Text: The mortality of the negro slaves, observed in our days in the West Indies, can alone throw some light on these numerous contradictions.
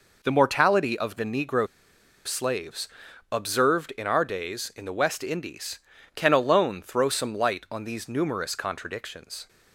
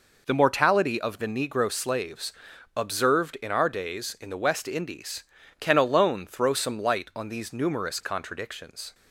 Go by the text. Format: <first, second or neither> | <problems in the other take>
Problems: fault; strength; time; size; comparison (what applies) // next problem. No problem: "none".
second | pauses between "negro" and "slaves"; noticeable; at 1.6 s; 0.58 s long